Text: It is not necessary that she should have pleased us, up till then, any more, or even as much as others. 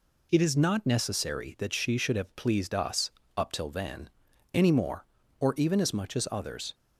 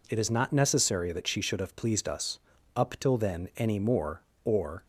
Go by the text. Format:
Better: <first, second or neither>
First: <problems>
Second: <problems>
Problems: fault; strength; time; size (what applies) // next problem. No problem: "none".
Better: first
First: none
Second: stops before "even as much as others"; at 4.8 s